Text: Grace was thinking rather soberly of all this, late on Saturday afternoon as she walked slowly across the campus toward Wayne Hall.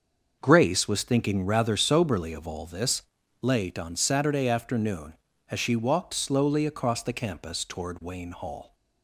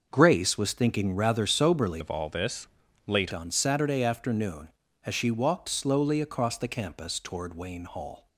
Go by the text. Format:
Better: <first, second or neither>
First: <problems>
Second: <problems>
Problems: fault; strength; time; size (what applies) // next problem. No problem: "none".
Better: first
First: starts louder than the rest; until 1.4 s; 6.5 dB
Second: starts louder than the rest; until 1.1 s; 6 dB // changes voice from "of" to "late"; from 2.0 to 3.3 s; 1.3 s long